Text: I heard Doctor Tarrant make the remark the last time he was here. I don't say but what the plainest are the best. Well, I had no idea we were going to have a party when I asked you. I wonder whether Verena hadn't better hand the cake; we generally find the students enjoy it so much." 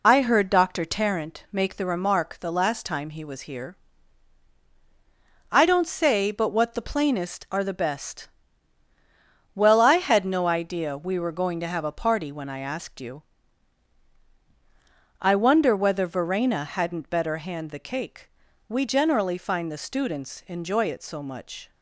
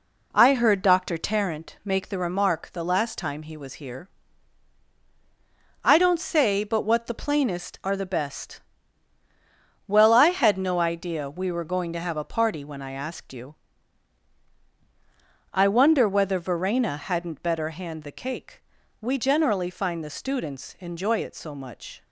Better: second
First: loses the start of "I"; at 0.0 s; 45 ms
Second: none

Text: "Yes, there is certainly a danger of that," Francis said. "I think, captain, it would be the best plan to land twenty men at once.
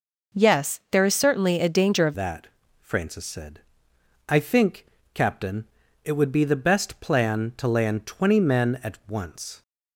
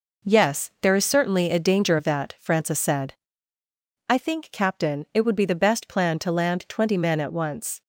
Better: second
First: changes voice at "that"; from 2.1 s on; 7.5 s long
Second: none

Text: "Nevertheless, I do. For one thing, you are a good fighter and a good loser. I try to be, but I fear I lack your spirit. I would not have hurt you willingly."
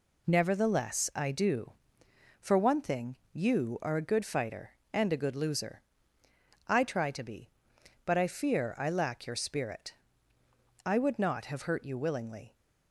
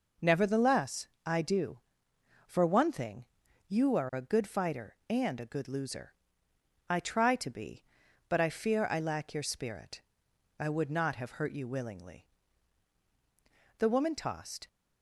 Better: first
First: none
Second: goes on to say "The woman tossed"; noticeable; from 13.7 s on; 0.88 s long

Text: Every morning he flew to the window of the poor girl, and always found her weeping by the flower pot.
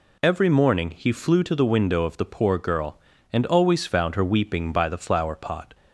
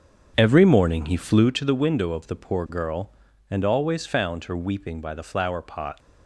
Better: first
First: none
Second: starts louder than the rest; strong; until 1.6 s; 7.5 dB

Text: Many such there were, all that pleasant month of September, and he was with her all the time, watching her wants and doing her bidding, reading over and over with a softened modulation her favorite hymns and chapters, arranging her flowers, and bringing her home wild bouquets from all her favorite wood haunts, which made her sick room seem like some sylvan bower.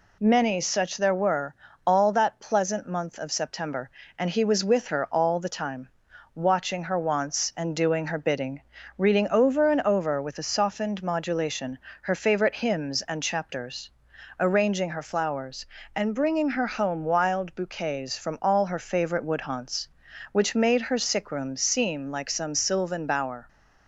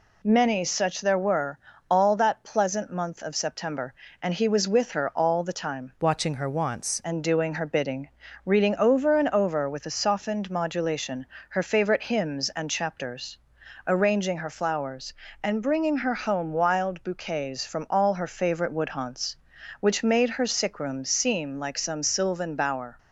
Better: first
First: pauses between "modulation" and "her"; slight; at 11.7 s; 0.24 s long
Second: changes voice from "watching" to "wants"; from 6.0 to 7.0 s; 1.0 s long // pauses between "modulation" and "her"; slight; at 11.2 s; 0.24 s long

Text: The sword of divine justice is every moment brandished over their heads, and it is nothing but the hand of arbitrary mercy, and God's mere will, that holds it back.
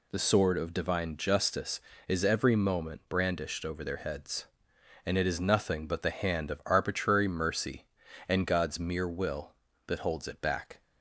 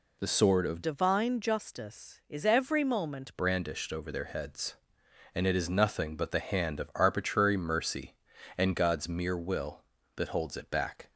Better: first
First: none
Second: changes voice from "divine" to "moment"; from 0.8 to 3.3 s; 2.5 s long

